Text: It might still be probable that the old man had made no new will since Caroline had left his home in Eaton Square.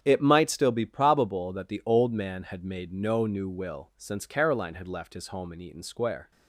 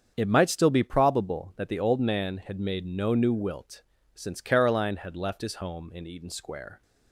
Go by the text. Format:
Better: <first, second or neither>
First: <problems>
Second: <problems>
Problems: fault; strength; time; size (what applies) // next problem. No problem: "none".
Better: first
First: starts louder than the rest; strong; until 1.0 s; 8 dB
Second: starts louder than the rest; strong; until 1.1 s; 7.5 dB // says "wilt" for "will"; at 3.3 s